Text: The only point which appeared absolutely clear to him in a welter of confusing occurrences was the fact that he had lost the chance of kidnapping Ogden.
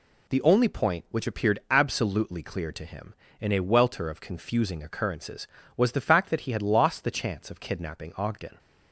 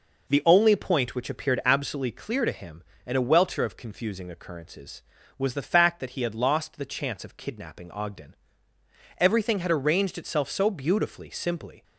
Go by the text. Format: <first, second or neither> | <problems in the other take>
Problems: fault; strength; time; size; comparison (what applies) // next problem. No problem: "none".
first | goes on to say "Everything had arranged itself so beautifully simply"; strong; from 9.1 s on; 2.6 s long